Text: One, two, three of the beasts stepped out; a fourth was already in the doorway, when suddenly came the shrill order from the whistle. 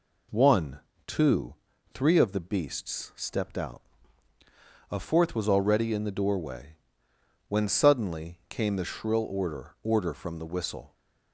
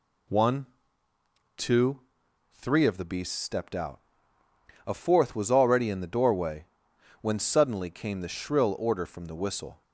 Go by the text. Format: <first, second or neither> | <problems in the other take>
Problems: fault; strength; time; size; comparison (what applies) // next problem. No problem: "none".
second | says "order" twice; at 9.8 s